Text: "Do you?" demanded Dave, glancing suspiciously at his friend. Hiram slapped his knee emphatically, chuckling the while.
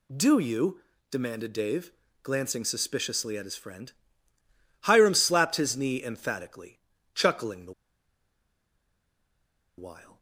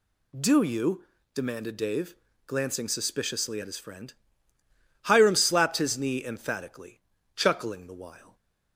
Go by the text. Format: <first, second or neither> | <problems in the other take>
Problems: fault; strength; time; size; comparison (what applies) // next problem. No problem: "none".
second | pauses between "the" and "while"; strong; at 7.7 s; 2.0 s long